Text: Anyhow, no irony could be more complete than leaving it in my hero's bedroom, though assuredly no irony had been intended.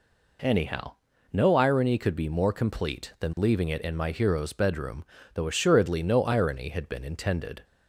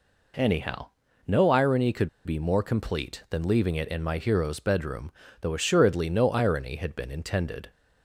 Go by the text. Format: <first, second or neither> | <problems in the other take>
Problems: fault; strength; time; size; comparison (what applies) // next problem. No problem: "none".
first | pauses between "could" and "be"; slight; at 2.0 s; 0.16 s long